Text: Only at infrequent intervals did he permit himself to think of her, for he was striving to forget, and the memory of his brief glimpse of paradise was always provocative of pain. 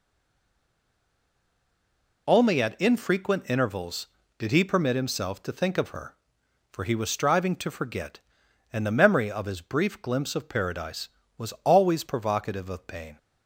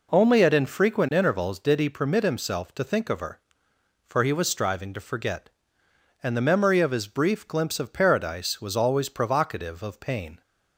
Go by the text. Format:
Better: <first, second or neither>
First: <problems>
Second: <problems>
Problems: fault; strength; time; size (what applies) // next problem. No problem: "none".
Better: second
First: stays silent before the first word; until 2.2 s; 2.2 s long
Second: none